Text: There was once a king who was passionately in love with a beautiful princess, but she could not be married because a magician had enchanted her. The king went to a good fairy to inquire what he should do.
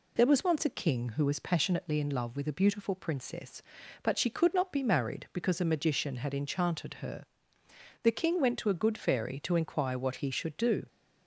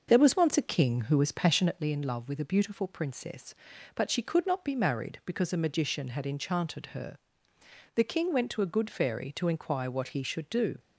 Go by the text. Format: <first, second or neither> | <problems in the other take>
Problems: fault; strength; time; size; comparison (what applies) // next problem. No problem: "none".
first | starts louder than the rest; noticeable; until 1.9 s; 6 dB